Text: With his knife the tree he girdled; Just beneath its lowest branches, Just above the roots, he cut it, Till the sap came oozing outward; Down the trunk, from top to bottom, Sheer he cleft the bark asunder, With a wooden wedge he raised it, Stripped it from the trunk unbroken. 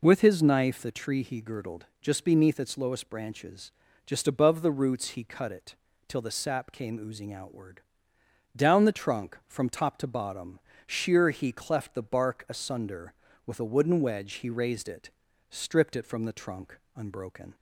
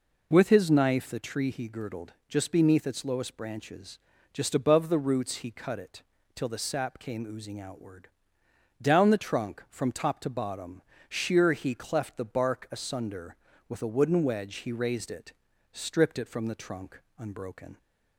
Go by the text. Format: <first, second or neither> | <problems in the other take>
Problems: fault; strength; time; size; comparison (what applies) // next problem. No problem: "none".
neither | pauses between "trunk" and "unbroken"; slight; the same in both